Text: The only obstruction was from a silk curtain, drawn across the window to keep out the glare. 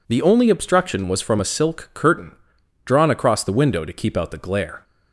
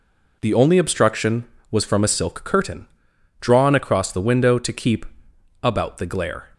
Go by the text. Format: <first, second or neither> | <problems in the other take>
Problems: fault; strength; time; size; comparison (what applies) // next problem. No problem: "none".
first | says "about" for "out"; at 5.6 s